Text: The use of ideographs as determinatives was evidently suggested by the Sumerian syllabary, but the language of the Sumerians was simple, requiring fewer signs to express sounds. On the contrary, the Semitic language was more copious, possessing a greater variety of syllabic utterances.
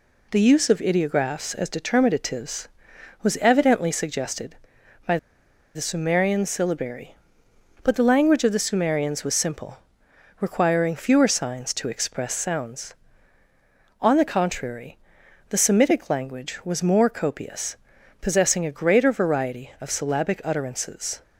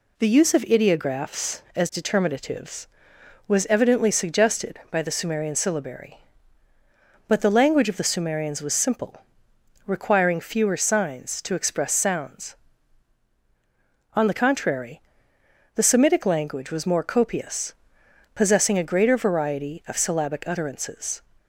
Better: second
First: pauses between "by" and "the"; noticeable; at 5.1 s; 0.58 s long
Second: none

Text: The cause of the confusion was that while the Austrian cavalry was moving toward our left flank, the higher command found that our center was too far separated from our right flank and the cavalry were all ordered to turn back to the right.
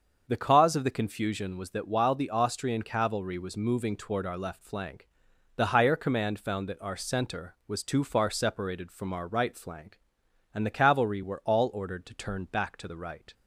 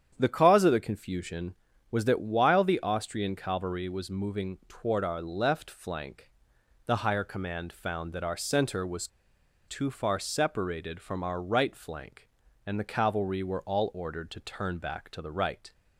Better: first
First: starts louder than the rest; until 1.2 s; 6.5 dB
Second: starts louder than the rest; strong; until 1.2 s; 9 dB // pauses between "was" and "too"; noticeable; at 9.0 s; 0.60 s long

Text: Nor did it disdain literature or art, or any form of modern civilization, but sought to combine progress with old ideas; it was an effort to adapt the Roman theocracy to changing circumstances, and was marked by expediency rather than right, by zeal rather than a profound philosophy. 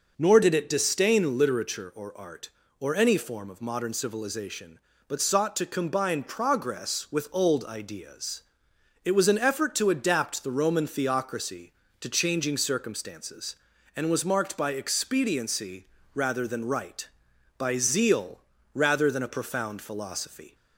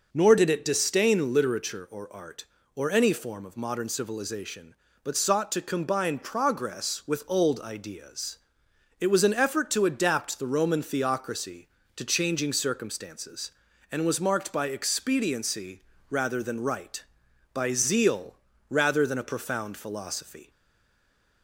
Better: first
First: pauses between "expediency" and "rather"; slight; at 15.8 s; 0.26 s long // pauses between "zeal" and "rather"; slight; at 18.3 s; 0.34 s long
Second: pauses between "expediency" and "rather"; slight; at 15.8 s; 0.26 s long // pauses between "zeal" and "rather"; slight; at 18.3 s; 0.34 s long // stays silent after the last word; from 20.5 s on; 0.9 s long

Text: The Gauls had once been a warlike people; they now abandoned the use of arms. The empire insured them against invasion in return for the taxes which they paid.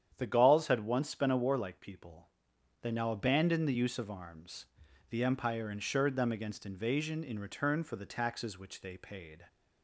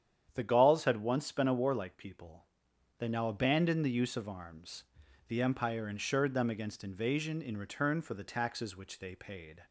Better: neither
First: starts louder than the rest; strong; until 1.1 s; 9 dB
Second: starts louder than the rest; strong; until 1.3 s; 9 dB

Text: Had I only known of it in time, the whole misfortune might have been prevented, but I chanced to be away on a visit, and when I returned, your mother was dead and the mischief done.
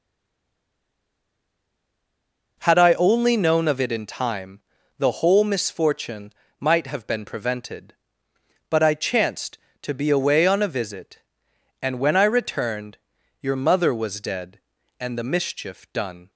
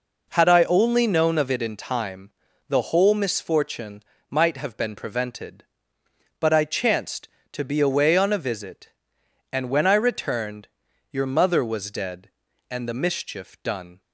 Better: second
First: stays silent before the first word; strong; until 2.5 s; 2.5 s long // pauses between "misfortune" and "might"; slight; at 6.3 s; 0.28 s long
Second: pauses between "misfortune" and "might"; slight; at 4.0 s; 0.28 s long

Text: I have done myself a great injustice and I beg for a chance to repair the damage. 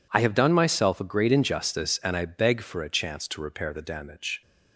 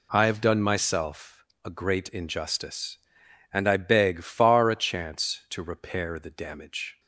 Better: first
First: none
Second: pauses between "myself" and "a"; slight; at 1.4 s; 0.20 s long // says "far" for "for"; at 4.2 s

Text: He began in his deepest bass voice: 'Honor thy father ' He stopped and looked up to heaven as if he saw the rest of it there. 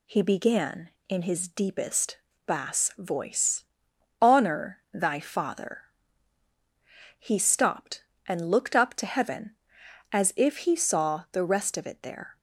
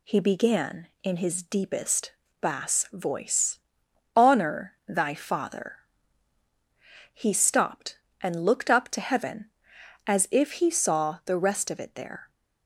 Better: neither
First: pauses between "deepest" and "bass"; slight; at 2.1 s; 0.30 s long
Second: pauses between "deepest" and "bass"; slight; at 2.1 s; 0.30 s long

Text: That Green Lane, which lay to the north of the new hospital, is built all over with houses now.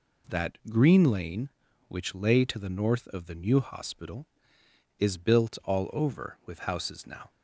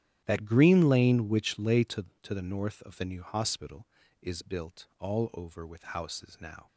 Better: first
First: none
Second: starts louder than the rest; strong; until 1.2 s; 11.5 dB // says "to" twice; at 2.2 s

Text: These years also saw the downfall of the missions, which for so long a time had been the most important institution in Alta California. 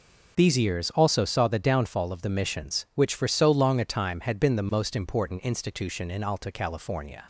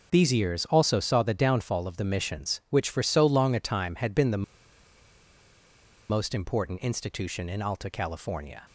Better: first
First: none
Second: pauses between "the" and "most"; strong; at 4.4 s; 1.6 s long

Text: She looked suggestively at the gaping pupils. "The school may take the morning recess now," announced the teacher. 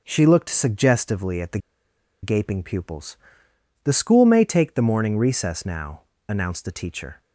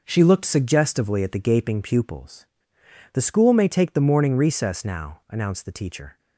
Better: second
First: pauses between "the" and "gaping"; noticeable; at 1.5 s; 0.64 s long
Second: none

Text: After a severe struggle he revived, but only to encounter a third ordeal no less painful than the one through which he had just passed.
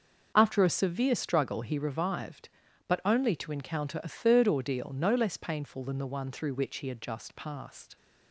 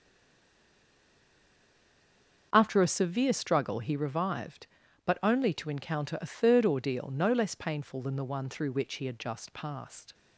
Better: first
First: starts louder than the rest; until 1.3 s; 6.5 dB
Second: stays silent before the first word; until 2.5 s; 2.5 s long // starts louder than the rest; until 3.5 s; 6.5 dB

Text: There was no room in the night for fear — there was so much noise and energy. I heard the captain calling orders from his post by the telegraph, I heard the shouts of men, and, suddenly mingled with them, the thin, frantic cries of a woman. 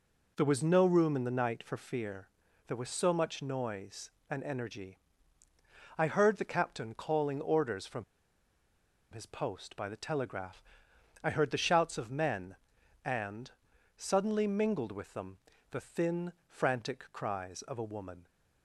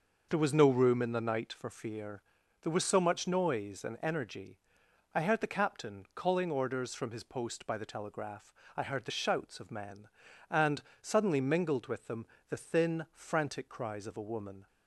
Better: second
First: pauses between "from" and "his"; at 8.0 s; 1.0 s long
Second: none

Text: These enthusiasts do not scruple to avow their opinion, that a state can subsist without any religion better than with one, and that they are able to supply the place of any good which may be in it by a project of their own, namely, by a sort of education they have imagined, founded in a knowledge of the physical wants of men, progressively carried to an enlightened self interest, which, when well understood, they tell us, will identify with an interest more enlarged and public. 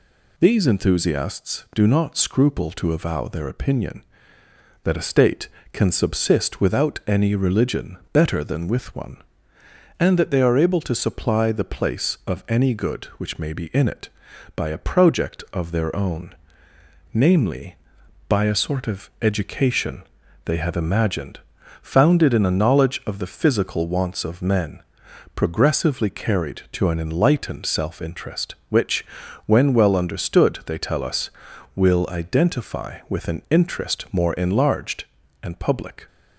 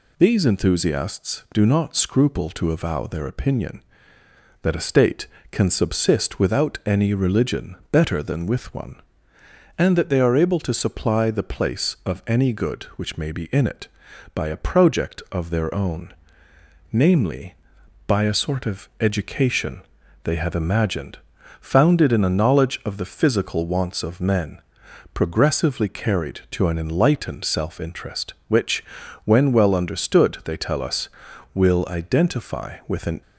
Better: first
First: pauses between "religion" and "better"; slight; at 7.9 s; 0.16 s long // pauses between "education" and "they"; at 20.0 s; 0.42 s long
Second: pauses between "religion" and "better"; slight; at 7.7 s; 0.16 s long // pauses between "education" and "they"; at 19.8 s; 0.42 s long // stops before "interest more enlarged and public"; at 33.2 s

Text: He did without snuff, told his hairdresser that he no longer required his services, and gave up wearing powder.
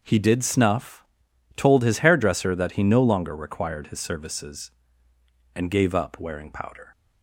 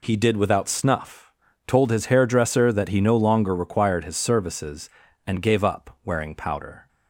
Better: second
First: skips "without"; at 0.4 s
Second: none

